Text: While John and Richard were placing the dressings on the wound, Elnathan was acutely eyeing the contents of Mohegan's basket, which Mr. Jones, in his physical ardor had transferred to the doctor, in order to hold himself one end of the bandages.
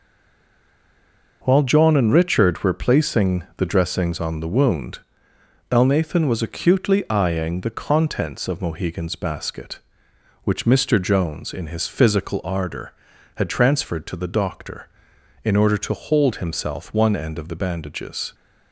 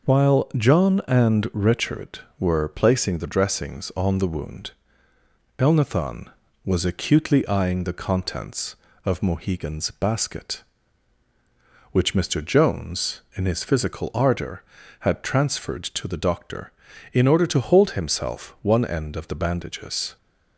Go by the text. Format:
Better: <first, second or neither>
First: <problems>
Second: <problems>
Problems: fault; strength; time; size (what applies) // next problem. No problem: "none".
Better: second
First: stays silent before the first word; noticeable; until 1.4 s; 1.4 s long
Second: none